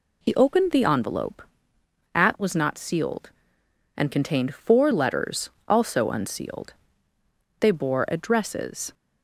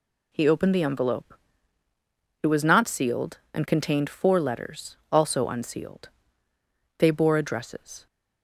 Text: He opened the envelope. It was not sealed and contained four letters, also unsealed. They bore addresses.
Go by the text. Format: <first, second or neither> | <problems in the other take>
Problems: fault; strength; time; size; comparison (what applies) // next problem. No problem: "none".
second | says "At" for "It"; at 2.1 s